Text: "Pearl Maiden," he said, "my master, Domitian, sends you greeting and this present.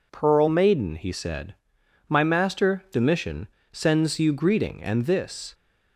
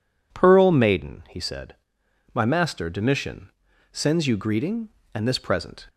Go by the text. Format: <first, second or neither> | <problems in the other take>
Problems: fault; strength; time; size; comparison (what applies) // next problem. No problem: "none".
second | stops before "present"; at 5.5 s